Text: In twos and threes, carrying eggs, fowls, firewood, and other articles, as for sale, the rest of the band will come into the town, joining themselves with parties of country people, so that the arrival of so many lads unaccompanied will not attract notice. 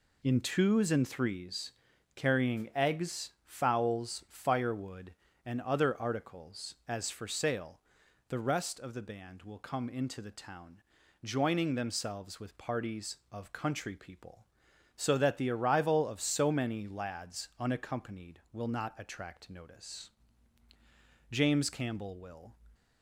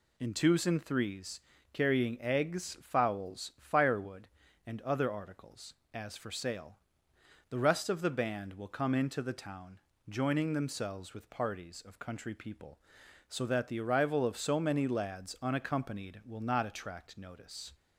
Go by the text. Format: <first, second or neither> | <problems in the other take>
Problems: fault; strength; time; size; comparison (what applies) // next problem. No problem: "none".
second | goes on to say "James Campbell will"; noticeable; from 21.3 s on; 1.2 s long